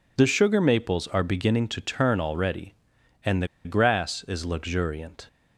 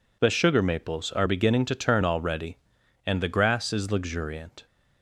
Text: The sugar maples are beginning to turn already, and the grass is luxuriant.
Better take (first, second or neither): second